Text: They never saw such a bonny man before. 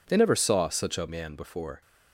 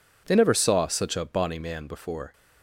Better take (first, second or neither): second